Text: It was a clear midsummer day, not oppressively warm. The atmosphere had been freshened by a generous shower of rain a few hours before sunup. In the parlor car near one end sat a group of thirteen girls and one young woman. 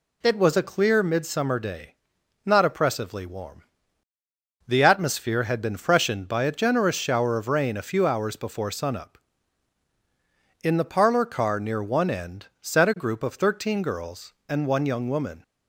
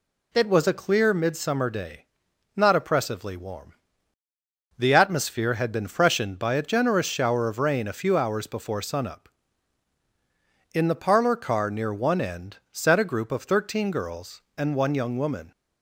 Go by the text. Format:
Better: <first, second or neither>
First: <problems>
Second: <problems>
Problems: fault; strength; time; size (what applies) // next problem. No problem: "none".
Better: neither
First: none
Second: none